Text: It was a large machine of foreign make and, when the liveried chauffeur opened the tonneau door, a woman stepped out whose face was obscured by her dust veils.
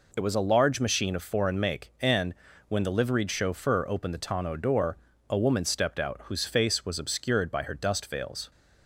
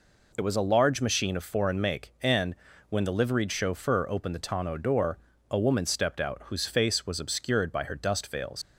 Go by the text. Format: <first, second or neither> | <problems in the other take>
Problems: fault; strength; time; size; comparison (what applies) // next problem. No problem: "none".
first | leaves "veils" unfinished; at 8.6 s; 95 ms